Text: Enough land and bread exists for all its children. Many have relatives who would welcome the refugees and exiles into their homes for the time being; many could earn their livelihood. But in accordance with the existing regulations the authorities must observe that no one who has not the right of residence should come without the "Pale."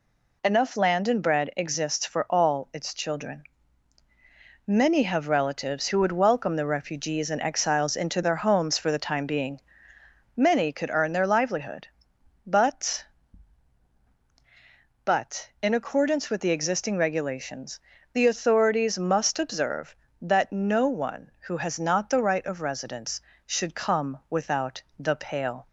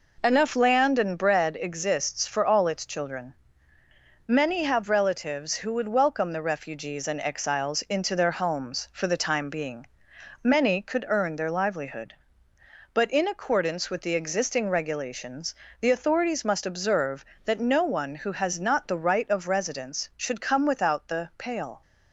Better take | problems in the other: second | says "But" twice; at 15.0 s // pauses between "regulations" and "the"; slight; at 17.8 s; 0.32 s long; slight in the second

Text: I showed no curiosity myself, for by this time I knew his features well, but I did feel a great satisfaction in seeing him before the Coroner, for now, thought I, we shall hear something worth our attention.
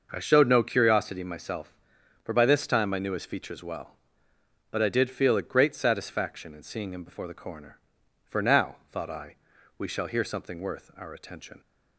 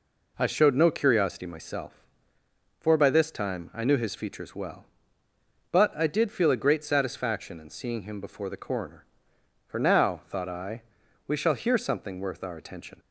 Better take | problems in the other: neither | none

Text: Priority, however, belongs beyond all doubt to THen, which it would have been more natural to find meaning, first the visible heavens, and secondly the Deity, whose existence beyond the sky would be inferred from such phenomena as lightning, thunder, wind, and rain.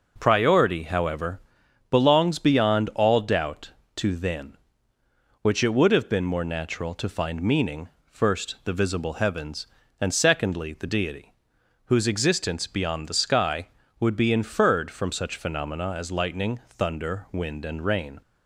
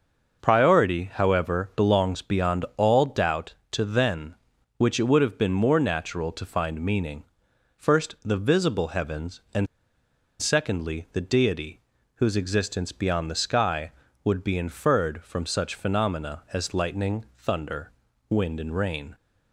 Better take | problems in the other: first | starts louder than the rest; noticeable; until 1.4 s; 6 dB // pauses between "and" and "secondly"; noticeable; at 9.6 s; 0.74 s long

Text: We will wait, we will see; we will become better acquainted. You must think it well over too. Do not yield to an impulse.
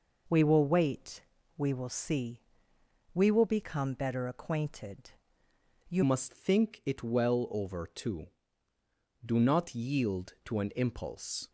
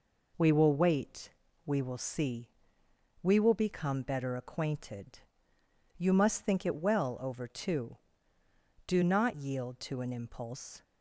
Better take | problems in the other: second | changes voice at "must"; from 6.0 s on; 5.4 s long

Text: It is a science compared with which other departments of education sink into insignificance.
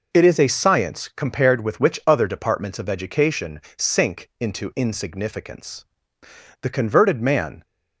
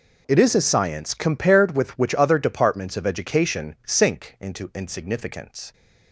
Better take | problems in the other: second | pauses between "education" and "sink"; slight; at 3.6 s; 0.16 s long // goes on to say "The converted man"; noticeable; from 6.6 s on; 1.0 s long

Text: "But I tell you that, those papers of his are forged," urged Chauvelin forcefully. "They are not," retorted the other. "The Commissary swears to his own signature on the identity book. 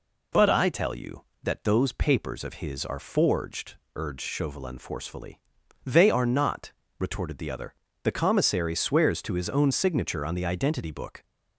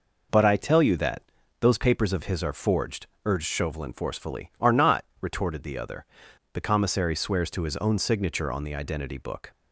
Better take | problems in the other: first | skips "They"; at 4.5 s

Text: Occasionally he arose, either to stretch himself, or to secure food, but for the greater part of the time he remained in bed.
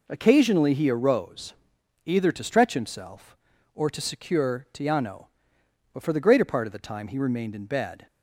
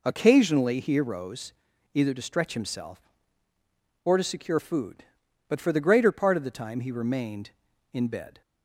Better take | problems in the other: second | says "tiano" for "food"; at 4.7 s

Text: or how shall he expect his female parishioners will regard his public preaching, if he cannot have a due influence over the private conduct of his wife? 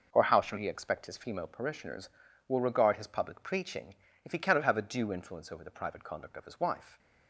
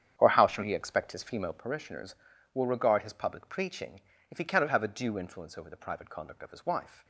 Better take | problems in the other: first | starts louder than the rest; strong; until 1.7 s; 9 dB

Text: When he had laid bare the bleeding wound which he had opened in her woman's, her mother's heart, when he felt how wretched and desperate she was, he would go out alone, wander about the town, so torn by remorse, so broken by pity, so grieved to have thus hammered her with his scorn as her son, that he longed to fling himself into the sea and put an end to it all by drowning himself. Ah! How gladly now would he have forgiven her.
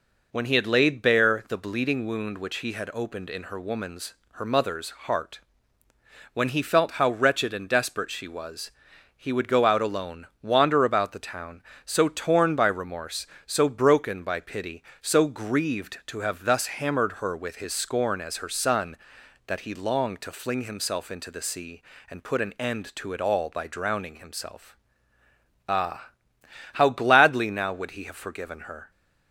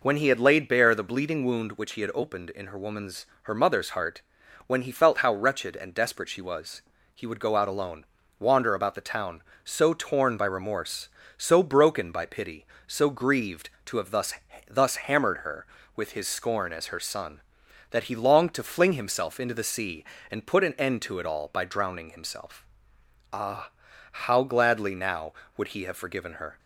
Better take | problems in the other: first | says "thus" twice; at 14.6 s

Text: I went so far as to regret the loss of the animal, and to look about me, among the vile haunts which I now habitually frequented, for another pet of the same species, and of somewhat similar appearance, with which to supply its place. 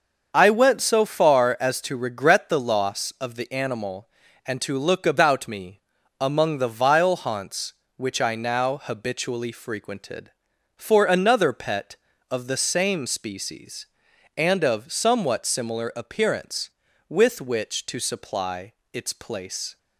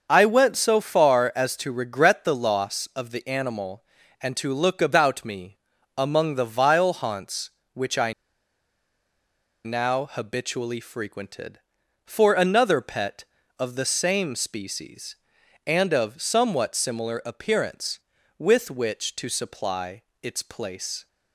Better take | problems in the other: first | starts louder than the rest; until 1.1 s; 6.5 dB; also in the first // pauses between "I" and "now"; strong; at 8.1 s; 1.5 s long // pauses between "supply" and "its"; slight; at 20.0 s; 0.18 s long; slight in the first

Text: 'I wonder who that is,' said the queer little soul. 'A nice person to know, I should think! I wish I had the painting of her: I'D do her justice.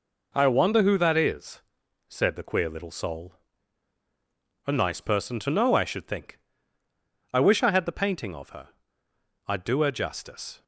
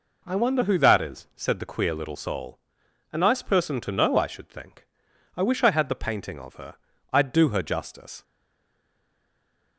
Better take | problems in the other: first | stays silent after the last word; noticeable; from 8.2 s on; 1.5 s long

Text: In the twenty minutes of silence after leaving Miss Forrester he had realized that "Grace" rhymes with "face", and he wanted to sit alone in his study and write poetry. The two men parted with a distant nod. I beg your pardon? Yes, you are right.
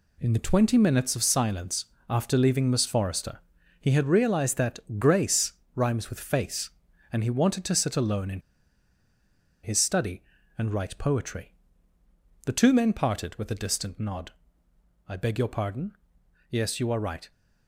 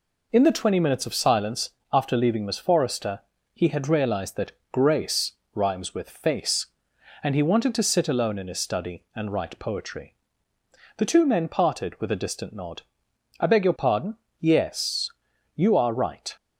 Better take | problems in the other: second | pauses between "silence" and "after"; slight; at 1.8 s; 0.24 s long; slight in the second // pauses between "Forrester" and "he"; at 3.3 s; 0.40 s long; slight in the second // pauses between "that" and "Grace"; slight; at 4.8 s; 0.18 s long; slight in the second // pauses between "Grace" and "rhymes"; slight; at 5.5 s; 0.24 s long; slight in the second // pauses between "in" and "his"; at 8.4 s; 1.2 s long

